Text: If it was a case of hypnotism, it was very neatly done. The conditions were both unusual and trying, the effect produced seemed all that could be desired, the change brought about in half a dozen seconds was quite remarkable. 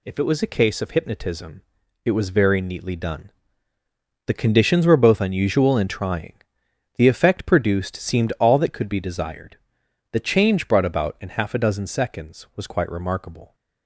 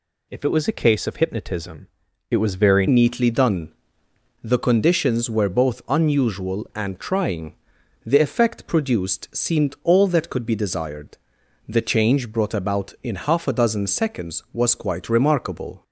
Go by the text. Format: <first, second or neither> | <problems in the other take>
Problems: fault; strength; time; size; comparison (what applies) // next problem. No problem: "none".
first | changes voice at "neatly"; from 2.8 s on; 13.0 s long